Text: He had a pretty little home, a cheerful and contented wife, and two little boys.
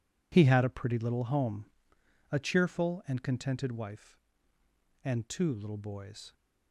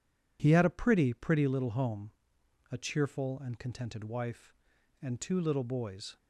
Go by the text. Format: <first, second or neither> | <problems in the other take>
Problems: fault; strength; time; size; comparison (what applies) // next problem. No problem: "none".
first | says "pretty" twice; at 1.1 s